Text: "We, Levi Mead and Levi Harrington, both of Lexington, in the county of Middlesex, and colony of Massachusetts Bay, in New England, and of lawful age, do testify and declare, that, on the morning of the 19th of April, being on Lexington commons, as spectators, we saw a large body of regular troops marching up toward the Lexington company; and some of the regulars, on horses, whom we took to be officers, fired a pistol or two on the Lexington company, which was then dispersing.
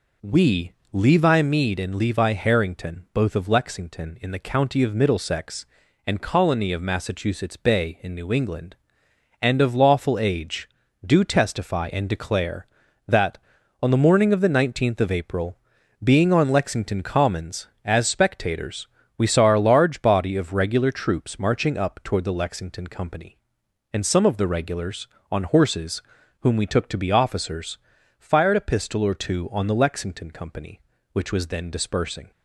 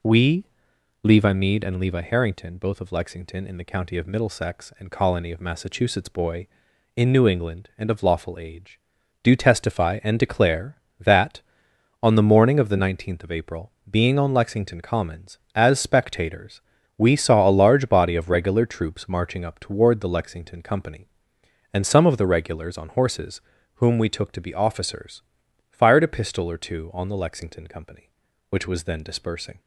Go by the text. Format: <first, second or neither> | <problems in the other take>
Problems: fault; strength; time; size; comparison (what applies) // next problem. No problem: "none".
first | says "Boy" for "Bay"; at 6.0 s